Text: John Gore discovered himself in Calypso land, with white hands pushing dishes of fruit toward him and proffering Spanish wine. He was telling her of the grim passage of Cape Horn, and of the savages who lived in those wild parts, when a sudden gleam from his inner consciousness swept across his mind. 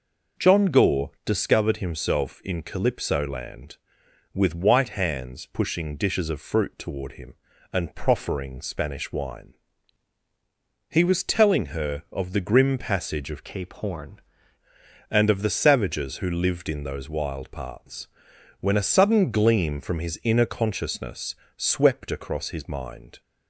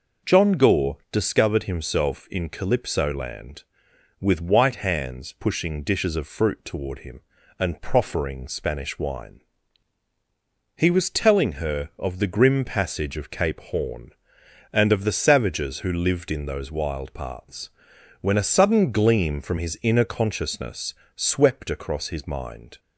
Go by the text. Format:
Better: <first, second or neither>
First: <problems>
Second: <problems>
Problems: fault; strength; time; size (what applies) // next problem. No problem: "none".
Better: second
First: changes voice from "Cape" to "Horn"; from 13.4 to 14.1 s; 0.7 s long // pauses between "consciousness" and "swept"; slight; at 21.3 s; 0.22 s long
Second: pauses between "consciousness" and "swept"; slight; at 20.9 s; 0.22 s long